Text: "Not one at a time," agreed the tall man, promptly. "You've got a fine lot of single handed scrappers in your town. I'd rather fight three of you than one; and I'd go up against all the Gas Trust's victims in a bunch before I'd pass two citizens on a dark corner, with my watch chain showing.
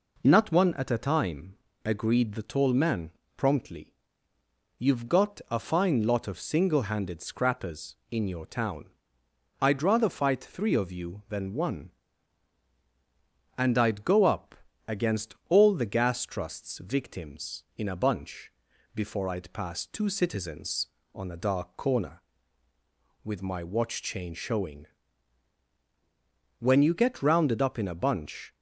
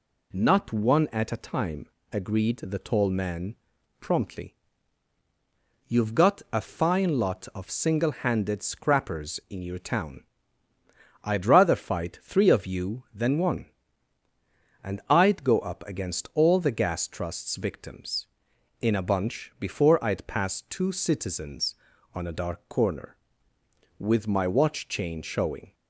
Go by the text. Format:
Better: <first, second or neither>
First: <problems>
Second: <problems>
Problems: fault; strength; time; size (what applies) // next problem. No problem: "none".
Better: second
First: pauses between "up" and "against"; slight; at 14.5 s; 0.32 s long // pauses between "bunch" and "before"; at 18.5 s; 0.44 s long // goes on to say "When you get rounded up in a bunch"; strong; from 26.5 s on; 1.9 s long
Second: none